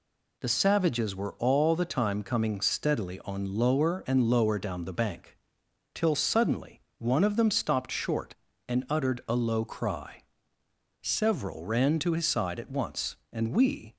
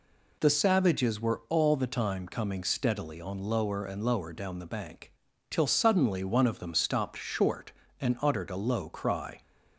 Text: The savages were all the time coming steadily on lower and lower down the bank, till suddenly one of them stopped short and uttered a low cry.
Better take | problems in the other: second | pauses between "suddenly" and "one"; slight; at 6.7 s; 0.20 s long // goes on to say "Several ran to his side at once and we"; strong; from 11.0 s on; 2.9 s long

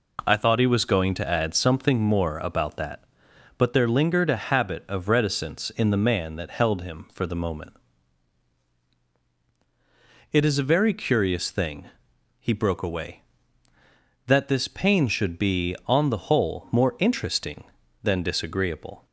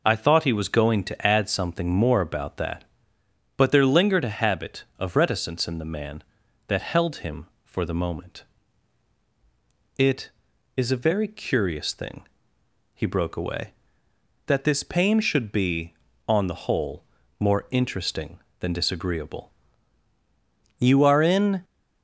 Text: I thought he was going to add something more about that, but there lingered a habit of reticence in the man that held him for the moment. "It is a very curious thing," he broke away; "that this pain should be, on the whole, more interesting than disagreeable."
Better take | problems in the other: first | goes on to say "You are in"; noticeable; from 20.7 s on; 0.86 s long

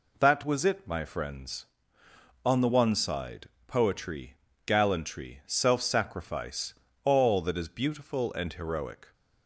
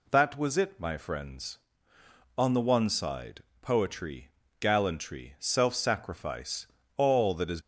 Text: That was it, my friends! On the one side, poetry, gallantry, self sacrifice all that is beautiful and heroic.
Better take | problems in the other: first | pauses between "sacrifice" and "all"; slight; at 6.6 s; 0.30 s long; slight in the first // stops before "beautiful and heroic"; at 7.6 s

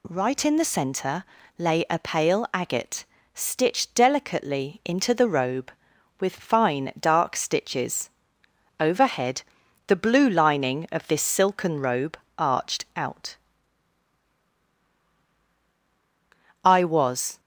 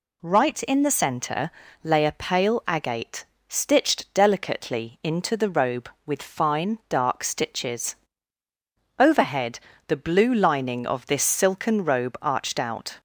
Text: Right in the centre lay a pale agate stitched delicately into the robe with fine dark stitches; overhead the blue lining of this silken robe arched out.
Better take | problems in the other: second | pauses between "centre" and "lay"; slight; at 1.2 s; 0.34 s long; slight in the second // pauses between "agate" and "stitched"; slight; at 3.0 s; 0.28 s long; slight in the second // pauses between "overhead" and "the"; noticeable; at 9.4 s; 0.46 s long; slight in the second // pauses between "robe" and "arched"; slight; at 12.1 s; 0.22 s long // goes on to say "I was"; noticeable; from 16.6 s on; 0.76 s long

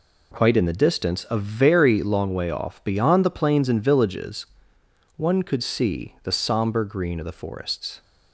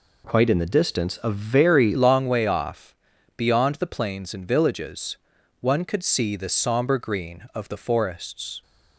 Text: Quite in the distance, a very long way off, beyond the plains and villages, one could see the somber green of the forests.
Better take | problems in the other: first | changes voice at "long"; from 1.9 s on; 6.7 s long

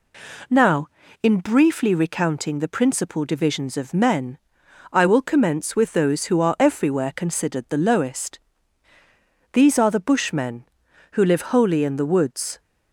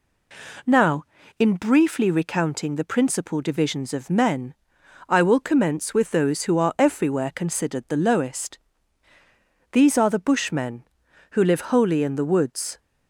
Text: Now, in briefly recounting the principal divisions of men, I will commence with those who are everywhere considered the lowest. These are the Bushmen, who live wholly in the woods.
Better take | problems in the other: neither | none

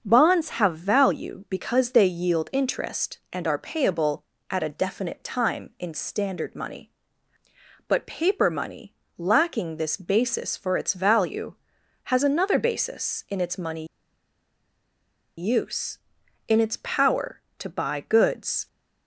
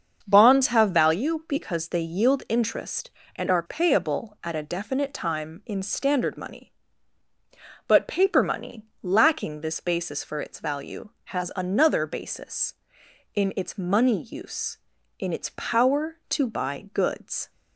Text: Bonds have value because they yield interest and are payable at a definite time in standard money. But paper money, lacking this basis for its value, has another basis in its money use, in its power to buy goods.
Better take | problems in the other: second | starts louder than the rest; until 1.0 s; 7 dB; also in the second // pauses between "money" and "use"; strong; at 13.8 s; 1.5 s long

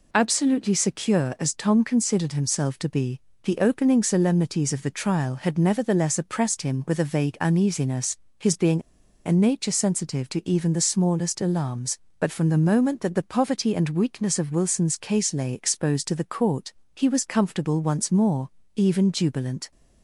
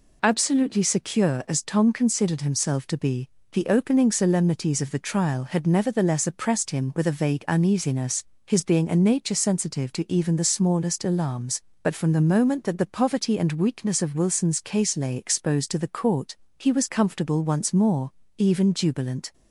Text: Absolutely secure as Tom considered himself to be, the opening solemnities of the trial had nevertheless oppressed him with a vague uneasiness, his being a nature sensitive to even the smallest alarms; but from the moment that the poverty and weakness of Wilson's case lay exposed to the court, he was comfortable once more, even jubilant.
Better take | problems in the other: second | pauses between "being" and "a"; at 8.8 s; 0.44 s long

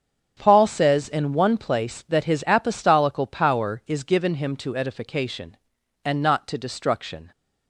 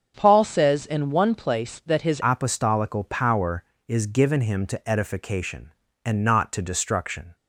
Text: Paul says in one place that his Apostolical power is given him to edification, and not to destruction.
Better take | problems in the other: first | starts louder than the rest; until 1.1 s; 7 dB; strong in the first // changes voice at "Apostolical"; from 2.2 s on; 5.1 s long

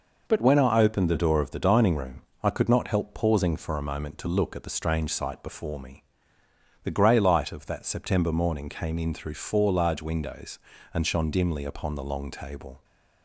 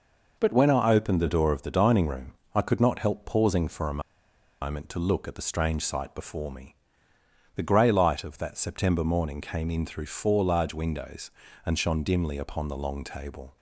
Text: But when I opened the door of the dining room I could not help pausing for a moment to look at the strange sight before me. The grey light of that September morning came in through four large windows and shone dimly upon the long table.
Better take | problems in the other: first | pauses between "room" and "I"; slight; at 2.3 s; 0.20 s long; slight in the first // pauses between "a" and "moment"; noticeable; at 4.0 s; 0.60 s long

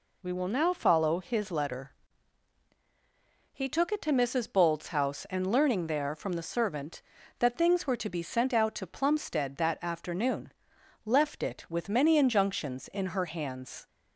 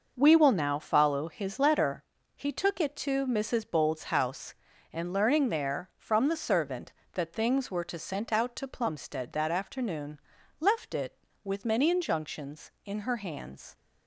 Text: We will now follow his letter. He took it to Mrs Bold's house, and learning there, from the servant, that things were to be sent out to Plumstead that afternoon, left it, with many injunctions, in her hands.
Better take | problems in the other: first | skips "be"; at 7.9 s

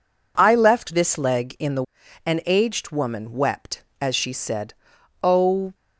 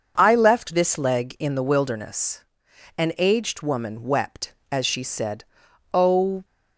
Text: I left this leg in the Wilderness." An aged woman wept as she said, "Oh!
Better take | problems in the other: second | skips "Wilderness"; at 2.0 s

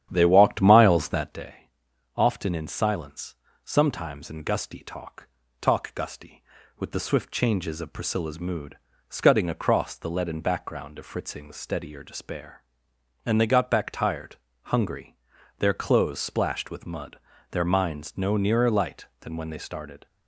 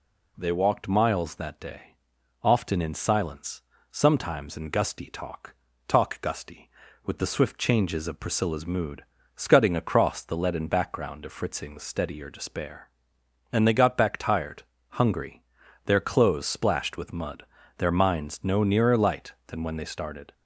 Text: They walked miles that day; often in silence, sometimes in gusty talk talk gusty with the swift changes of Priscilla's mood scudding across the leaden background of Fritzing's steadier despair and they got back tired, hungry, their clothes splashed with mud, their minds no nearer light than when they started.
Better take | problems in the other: second | starts louder than the rest; strong; until 1.5 s; 10 dB // pauses between "talk" and "talk"; slight; at 5.2 s; 0.34 s long; slight in the second // pauses between "mood" and "scudding"; slight; at 8.7 s; 0.30 s long; slight in the second

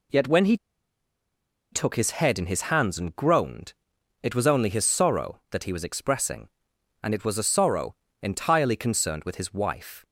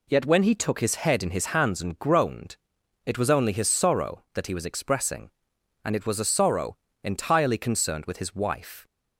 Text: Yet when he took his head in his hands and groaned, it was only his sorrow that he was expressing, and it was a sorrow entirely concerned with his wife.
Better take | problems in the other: second | pauses between "he" and "took"; at 0.5 s; 1.1 s long // pauses between "sorrow" and "entirely"; slight; at 7.9 s; 0.28 s long; slight in the second

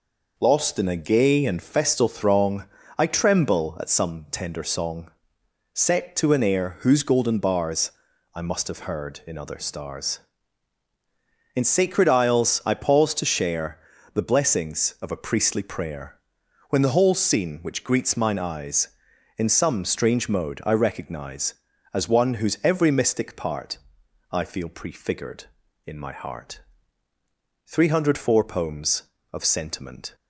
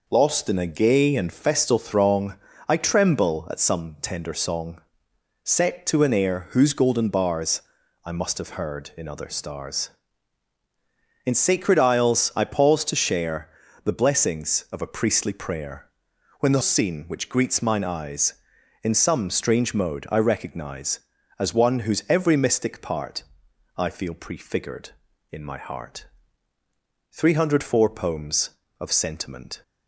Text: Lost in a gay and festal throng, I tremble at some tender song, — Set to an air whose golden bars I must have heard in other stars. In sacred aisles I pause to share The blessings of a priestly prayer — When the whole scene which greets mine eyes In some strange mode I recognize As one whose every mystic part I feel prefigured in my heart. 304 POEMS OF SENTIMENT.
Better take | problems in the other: first | pauses between "bars" and "I"; at 7.6 s; 0.44 s long; also in the first // pauses between "share" and "The"; slight; at 13.4 s; 0.34 s long; slight in the first // skips "whole"; at 16.6 s // pauses between "part" and "I"; noticeable; at 23.2 s; 0.52 s long; noticeable in the first

